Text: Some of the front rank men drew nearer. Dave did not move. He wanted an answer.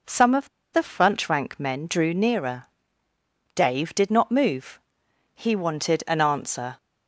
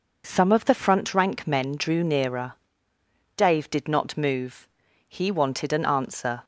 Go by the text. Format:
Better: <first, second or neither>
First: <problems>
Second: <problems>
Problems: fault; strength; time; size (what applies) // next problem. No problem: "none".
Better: second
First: pauses between "of" and "the"; slight; at 0.4 s; 0.24 s long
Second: none